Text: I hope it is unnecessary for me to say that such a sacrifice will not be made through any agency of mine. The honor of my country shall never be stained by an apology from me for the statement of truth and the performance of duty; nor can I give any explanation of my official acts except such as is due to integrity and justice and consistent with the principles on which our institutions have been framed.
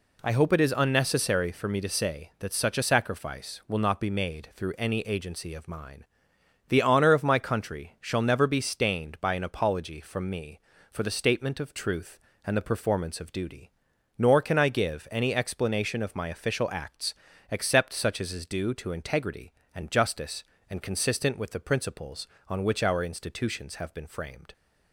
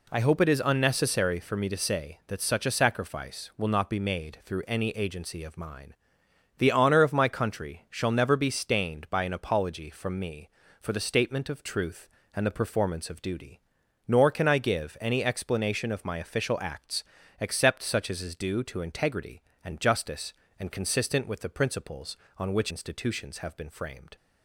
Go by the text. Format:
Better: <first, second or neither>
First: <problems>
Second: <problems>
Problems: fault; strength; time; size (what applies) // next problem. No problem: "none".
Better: first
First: pauses between "acts" and "except"; slight; at 17.1 s; 0.34 s long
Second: pauses between "acts" and "except"; slight; at 17.0 s; 0.34 s long // skips "our"; at 22.7 s